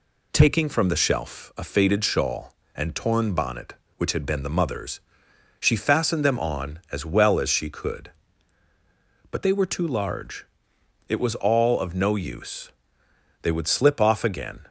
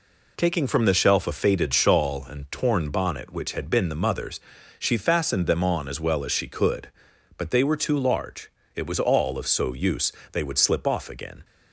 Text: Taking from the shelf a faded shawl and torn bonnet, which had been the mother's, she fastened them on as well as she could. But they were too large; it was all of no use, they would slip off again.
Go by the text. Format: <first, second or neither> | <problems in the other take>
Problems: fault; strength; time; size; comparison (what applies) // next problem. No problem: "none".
first | says "so" for "no"; at 9.4 s